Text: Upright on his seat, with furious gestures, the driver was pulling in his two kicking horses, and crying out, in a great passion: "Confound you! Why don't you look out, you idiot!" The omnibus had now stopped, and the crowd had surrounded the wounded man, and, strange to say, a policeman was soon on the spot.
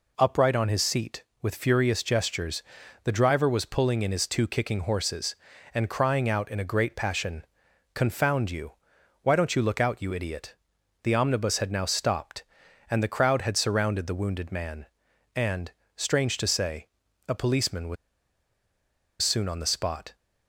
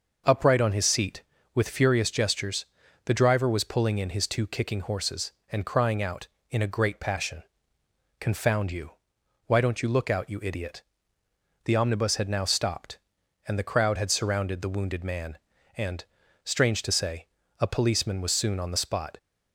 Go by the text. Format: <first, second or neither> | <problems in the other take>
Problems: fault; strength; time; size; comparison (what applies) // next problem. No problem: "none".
second | pauses between "was" and "soon"; strong; at 17.9 s; 1.2 s long